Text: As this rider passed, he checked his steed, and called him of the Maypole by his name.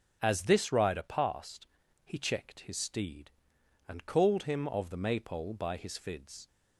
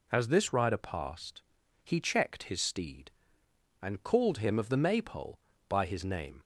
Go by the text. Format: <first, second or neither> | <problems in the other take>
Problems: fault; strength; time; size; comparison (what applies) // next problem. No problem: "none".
second | says "fids" for "name"; at 5.9 s